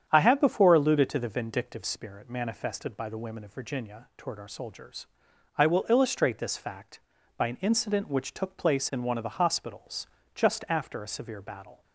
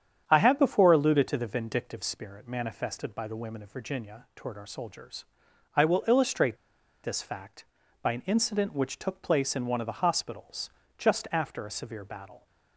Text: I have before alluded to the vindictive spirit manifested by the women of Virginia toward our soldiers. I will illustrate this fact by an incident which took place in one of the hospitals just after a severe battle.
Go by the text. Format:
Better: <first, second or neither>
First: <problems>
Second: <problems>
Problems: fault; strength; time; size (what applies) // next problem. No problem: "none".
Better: first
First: starts louder than the rest; strong; until 1.0 s; 8.5 dB // pauses between "hospitals" and "just"; slight; at 10.0 s; 0.26 s long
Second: starts louder than the rest; strong; until 1.2 s; 8.5 dB // pauses between "illustrate" and "this"; noticeable; at 6.5 s; 0.48 s long // pauses between "hospitals" and "just"; slight; at 10.7 s; 0.26 s long